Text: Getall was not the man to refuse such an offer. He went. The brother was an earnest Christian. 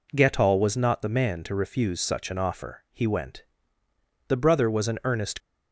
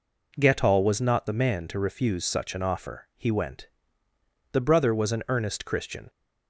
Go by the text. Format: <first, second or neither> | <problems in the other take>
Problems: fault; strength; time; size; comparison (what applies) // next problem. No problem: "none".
second | stops before "Christian"; at 5.3 s